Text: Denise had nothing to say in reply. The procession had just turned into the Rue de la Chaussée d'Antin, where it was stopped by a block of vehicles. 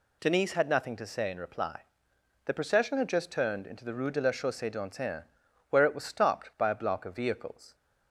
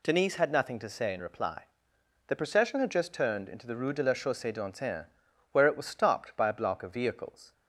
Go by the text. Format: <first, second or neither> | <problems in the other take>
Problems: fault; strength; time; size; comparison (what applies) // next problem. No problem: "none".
neither | none